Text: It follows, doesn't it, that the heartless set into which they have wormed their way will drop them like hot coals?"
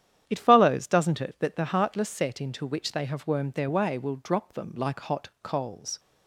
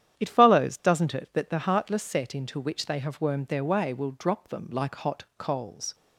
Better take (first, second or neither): neither